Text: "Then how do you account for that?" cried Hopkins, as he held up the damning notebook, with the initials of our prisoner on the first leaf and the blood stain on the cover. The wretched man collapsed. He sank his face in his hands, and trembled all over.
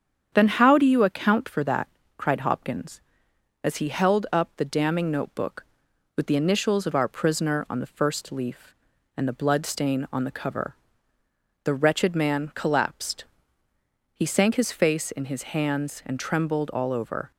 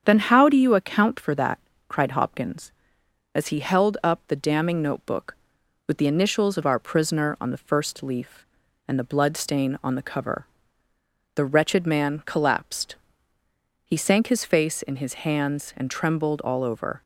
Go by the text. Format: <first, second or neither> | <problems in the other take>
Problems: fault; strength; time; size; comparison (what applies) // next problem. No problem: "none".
neither | starts louder than the rest; strong; the same in both